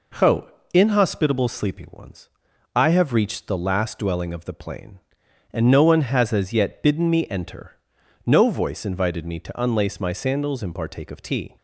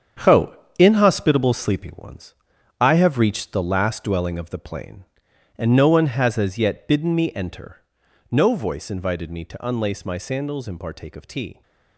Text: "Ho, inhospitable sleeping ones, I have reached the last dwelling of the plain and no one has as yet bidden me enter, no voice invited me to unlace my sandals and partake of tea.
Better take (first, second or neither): first